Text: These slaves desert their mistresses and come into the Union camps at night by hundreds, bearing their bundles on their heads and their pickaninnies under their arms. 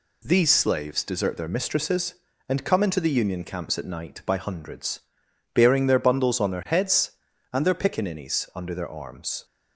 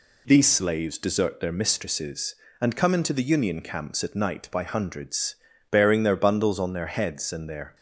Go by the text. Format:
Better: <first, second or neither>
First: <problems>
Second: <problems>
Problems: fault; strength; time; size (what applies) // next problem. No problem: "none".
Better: first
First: none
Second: stops before "pickaninnies under their arms"; at 7.7 s